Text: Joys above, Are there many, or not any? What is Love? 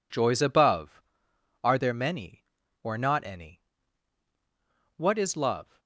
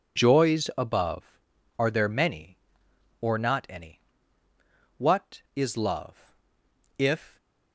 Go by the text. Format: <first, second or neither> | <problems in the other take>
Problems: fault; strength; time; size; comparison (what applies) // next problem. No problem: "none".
first | goes on to say "If"; slight; from 6.9 s on; 0.40 s long